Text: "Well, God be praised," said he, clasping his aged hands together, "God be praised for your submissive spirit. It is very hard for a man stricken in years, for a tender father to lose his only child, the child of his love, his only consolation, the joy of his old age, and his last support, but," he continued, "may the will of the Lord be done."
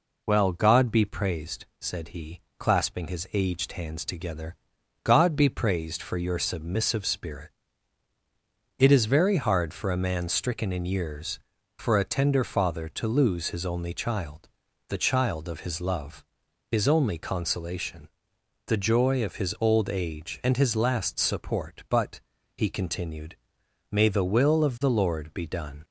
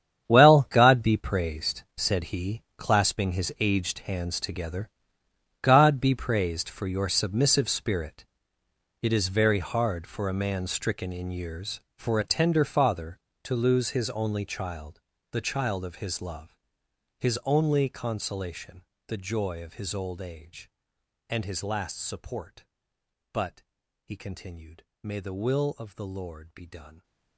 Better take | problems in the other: first | gets quieter; strong; throughout; 15 dB

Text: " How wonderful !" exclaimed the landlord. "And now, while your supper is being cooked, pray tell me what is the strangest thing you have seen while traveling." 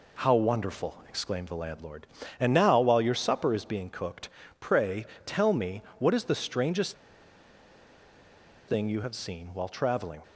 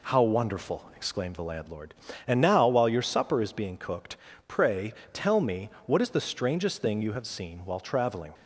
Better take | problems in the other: second | pauses between "pray" and "tell"; slight; at 5.0 s; 0.22 s long; slight in the second // pauses between "me" and "what"; slight; at 5.8 s; 0.16 s long; slight in the second // pauses between "strangest" and "thing"; strong; at 6.9 s; 1.7 s long

